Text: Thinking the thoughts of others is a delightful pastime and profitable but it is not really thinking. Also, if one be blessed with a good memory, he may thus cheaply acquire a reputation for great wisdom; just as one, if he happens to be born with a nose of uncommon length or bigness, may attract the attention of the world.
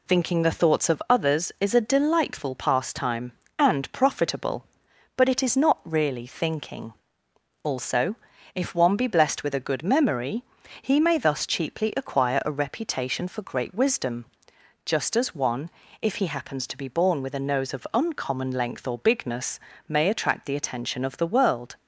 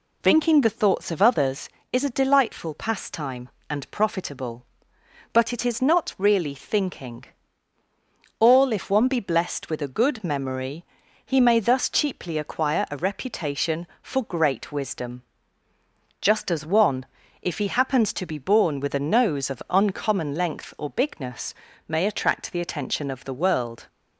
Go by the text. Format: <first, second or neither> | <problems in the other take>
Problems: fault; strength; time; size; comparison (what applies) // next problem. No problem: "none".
first | says "All" for "Also"; at 8.3 s